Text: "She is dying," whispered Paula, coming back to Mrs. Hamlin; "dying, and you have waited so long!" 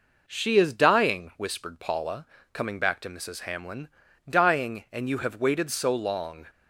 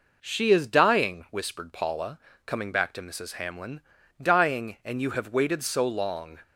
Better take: neither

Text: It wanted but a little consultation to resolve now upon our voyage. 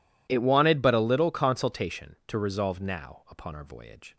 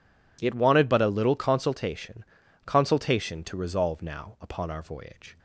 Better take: first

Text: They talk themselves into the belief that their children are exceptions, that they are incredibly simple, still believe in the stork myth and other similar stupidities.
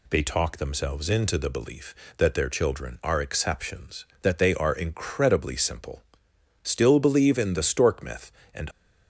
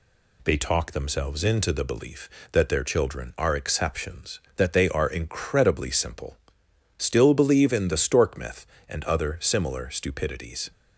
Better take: second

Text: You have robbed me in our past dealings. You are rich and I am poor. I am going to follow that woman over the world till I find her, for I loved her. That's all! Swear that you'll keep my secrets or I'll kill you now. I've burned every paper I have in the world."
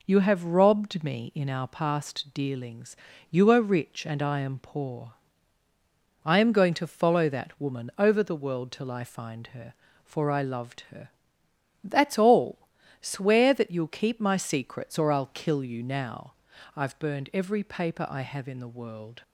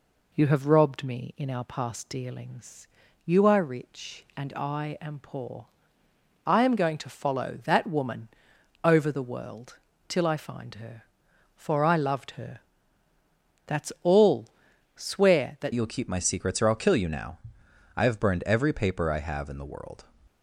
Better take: first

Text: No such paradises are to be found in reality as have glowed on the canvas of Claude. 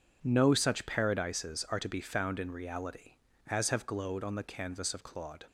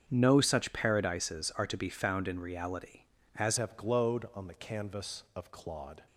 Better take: first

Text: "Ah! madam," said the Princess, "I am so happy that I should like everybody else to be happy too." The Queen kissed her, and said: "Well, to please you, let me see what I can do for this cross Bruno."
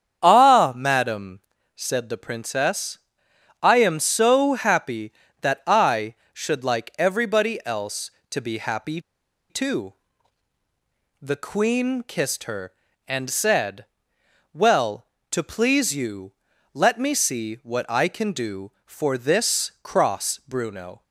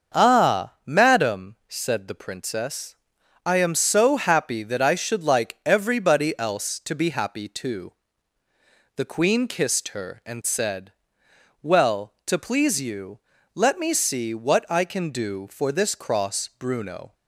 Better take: second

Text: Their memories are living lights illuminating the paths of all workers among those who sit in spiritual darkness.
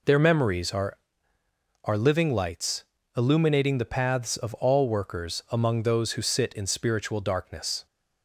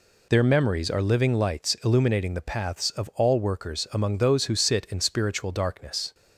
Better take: second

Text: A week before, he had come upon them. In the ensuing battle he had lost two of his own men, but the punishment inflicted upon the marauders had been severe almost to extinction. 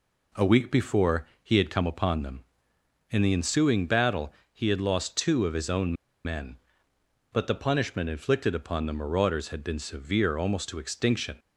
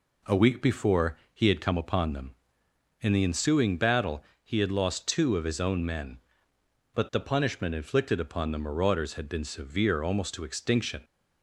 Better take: second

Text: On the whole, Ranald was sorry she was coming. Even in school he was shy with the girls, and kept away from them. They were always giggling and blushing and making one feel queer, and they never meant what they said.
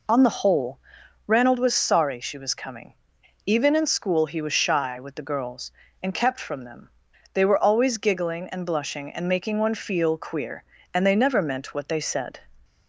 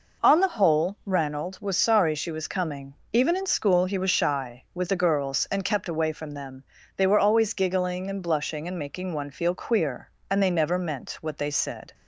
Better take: second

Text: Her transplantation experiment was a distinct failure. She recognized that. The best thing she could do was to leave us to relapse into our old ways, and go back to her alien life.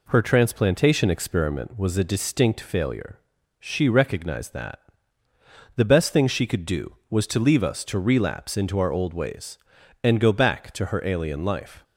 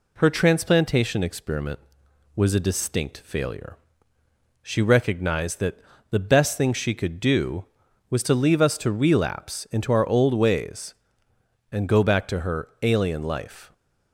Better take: neither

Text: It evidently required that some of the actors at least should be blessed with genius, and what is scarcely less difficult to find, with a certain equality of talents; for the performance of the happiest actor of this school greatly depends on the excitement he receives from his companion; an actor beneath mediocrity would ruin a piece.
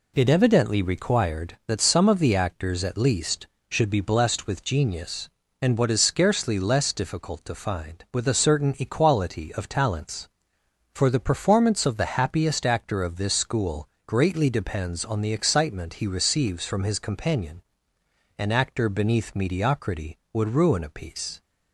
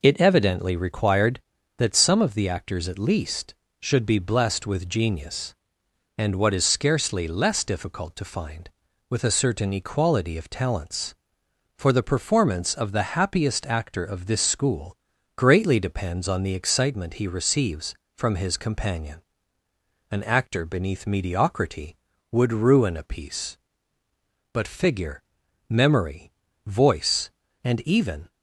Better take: first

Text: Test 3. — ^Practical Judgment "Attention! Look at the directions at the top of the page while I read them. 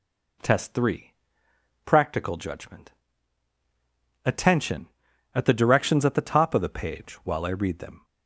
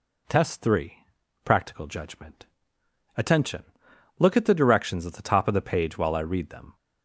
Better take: second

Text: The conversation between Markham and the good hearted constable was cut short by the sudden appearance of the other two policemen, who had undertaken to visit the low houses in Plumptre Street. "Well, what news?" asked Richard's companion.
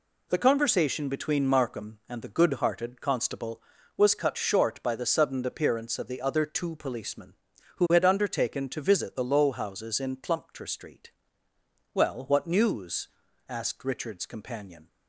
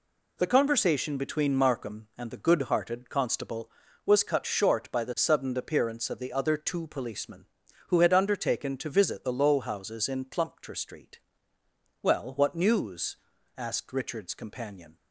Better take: neither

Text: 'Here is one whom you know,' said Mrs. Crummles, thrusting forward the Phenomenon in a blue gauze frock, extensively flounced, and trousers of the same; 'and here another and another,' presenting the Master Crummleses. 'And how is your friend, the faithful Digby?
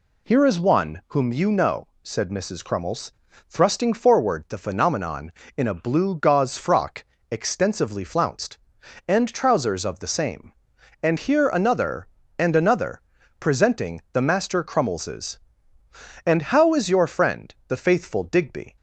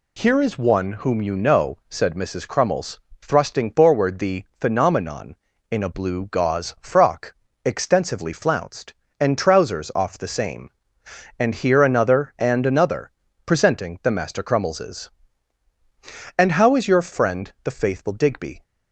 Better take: first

